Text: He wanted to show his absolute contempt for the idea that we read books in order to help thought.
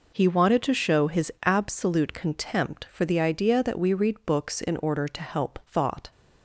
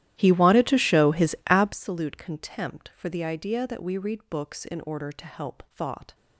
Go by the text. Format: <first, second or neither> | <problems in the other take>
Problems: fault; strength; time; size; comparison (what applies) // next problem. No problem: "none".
first | starts louder than the rest; strong; until 1.8 s; 13.5 dB